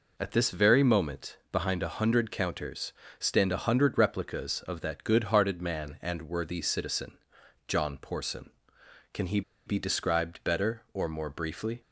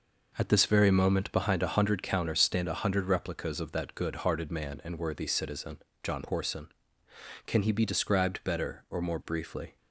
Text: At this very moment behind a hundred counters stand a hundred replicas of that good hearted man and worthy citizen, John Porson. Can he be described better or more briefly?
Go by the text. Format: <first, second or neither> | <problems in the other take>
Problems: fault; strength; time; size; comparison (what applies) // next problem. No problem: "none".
second | pauses between "counters" and "stand"; slight; at 2.9 s; 0.26 s long // pauses between "he" and "be"; slight; at 9.4 s; 0.25 s long